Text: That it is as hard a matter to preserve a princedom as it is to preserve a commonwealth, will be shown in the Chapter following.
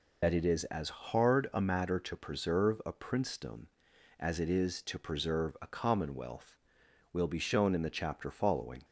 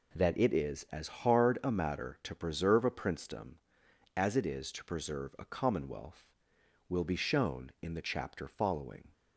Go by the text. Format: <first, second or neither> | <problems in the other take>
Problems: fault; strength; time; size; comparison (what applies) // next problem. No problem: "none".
second | loses the start of "That"; at 0.2 s; 40 ms